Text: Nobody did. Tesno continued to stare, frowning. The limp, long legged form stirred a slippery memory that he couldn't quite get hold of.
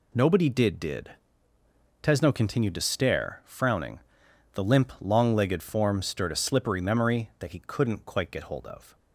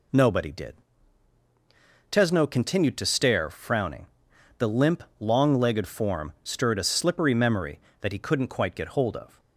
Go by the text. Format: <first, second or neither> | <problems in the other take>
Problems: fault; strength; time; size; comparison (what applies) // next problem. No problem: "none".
second | says "did" twice; at 0.7 s